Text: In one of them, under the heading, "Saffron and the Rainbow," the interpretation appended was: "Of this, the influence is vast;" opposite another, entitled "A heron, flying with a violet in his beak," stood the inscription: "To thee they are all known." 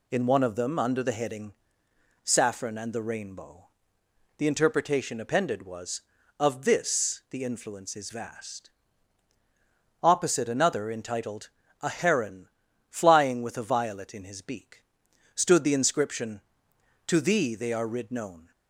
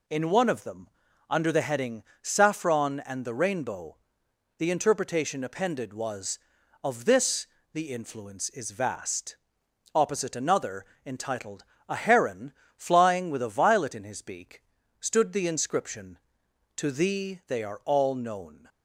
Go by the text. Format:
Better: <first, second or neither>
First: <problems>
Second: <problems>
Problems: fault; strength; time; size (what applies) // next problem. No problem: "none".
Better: second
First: pauses between "entitled" and "A"; slight; at 11.4 s; 0.32 s long // says "rid" for "all"; at 17.8 s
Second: pauses between "entitled" and "A"; slight; at 11.6 s; 0.24 s long